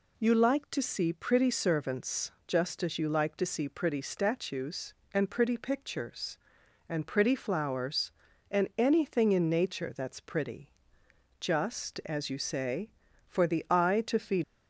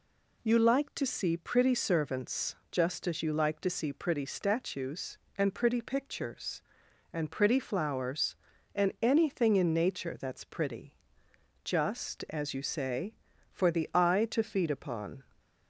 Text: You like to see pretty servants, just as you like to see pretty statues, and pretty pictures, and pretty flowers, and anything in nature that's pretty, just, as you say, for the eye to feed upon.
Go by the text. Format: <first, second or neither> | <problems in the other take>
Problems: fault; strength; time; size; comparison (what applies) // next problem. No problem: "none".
second | stops before "upon"; at 14.4 s